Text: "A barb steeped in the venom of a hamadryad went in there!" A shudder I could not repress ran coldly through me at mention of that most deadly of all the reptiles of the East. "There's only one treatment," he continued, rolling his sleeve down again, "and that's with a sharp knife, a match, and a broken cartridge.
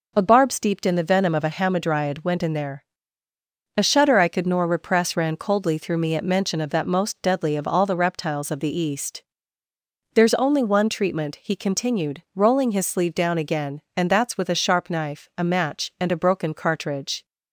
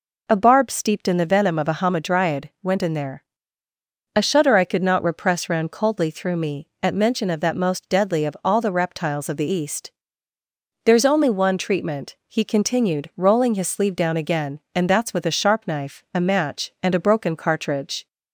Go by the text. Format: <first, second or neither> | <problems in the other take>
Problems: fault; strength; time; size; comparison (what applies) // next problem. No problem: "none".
second | says "nor" for "not"; at 4.4 s